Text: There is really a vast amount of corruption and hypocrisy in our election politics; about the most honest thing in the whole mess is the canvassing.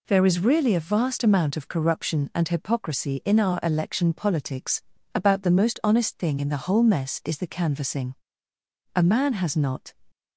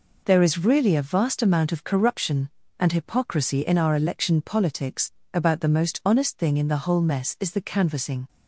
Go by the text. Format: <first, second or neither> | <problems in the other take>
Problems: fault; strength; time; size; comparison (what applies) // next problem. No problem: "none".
second | goes on to say "A man has not"; noticeable; from 8.9 s on; 0.98 s long